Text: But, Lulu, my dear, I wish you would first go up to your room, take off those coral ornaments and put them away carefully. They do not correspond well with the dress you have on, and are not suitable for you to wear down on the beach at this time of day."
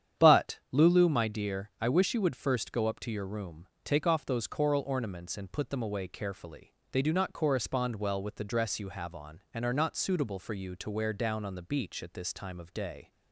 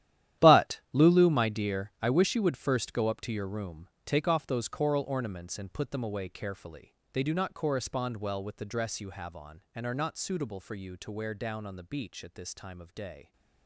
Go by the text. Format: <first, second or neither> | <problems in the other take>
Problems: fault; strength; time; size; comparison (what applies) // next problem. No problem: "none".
first | gets quieter; strong; throughout; 14.5 dB // starts louder than the rest; strong; until 1.5 s; 12 dB; strong in the first